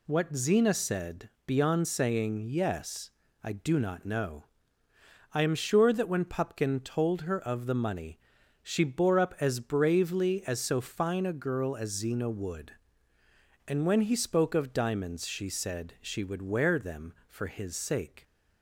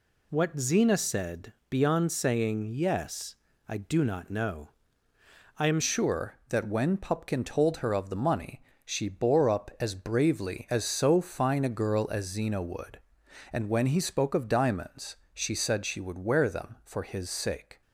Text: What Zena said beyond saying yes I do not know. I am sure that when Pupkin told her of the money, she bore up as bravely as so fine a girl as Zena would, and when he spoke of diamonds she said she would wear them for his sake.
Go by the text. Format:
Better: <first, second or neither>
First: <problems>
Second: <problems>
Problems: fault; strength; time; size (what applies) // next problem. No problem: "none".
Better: first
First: pauses between "said" and "beyond"; slight; at 1.2 s; 0.18 s long // pauses between "yes" and "I"; slight; at 3.1 s; 0.32 s long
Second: pauses between "said" and "beyond"; slight; at 1.5 s; 0.18 s long // pauses between "yes" and "I"; slight; at 3.3 s; 0.32 s long // changes voice at "sure"; from 5.8 s on; 12.0 s long // pauses between "diamonds" and "she"; slight; at 15.1 s; 0.16 s long